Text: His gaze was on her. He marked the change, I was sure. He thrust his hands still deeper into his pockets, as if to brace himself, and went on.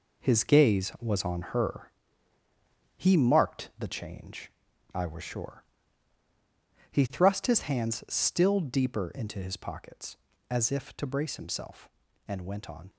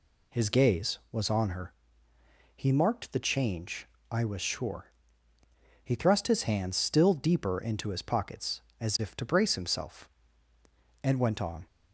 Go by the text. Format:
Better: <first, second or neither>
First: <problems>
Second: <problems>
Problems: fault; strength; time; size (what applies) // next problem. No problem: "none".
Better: second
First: gets quieter; strong; throughout; 8 dB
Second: none